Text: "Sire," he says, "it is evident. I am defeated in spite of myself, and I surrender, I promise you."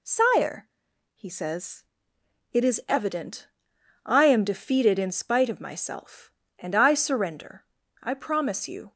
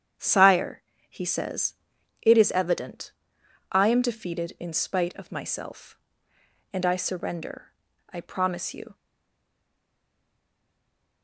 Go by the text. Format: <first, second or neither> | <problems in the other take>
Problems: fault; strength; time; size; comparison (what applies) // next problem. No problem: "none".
first | starts louder than the rest; strong; until 1.4 s; 9 dB // stays silent after the last word; from 8.9 s on; 2.3 s long